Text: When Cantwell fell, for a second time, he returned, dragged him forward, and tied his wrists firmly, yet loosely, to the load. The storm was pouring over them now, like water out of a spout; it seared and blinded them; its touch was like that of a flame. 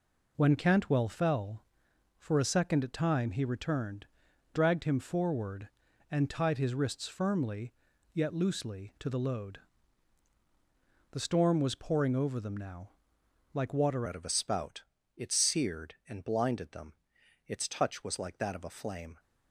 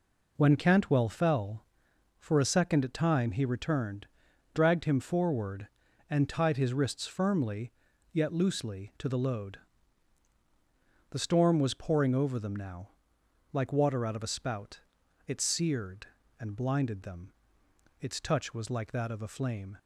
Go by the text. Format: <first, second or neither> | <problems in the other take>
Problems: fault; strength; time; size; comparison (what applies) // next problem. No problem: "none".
second | changes voice at "out"; from 14.0 s on; 5.1 s long